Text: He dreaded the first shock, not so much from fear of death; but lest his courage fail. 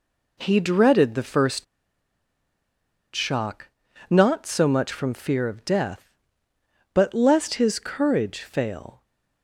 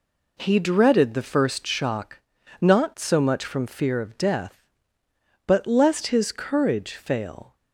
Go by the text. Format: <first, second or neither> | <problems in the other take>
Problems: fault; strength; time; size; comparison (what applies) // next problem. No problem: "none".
second | pauses between "first" and "shock"; strong; at 1.6 s; 1.4 s long